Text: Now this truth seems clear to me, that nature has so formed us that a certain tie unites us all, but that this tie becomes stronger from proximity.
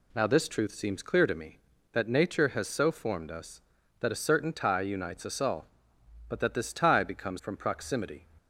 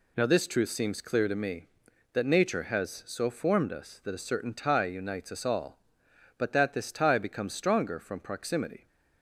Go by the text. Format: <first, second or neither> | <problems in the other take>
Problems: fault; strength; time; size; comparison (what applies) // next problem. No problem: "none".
second | skips "stronger"; at 7.3 s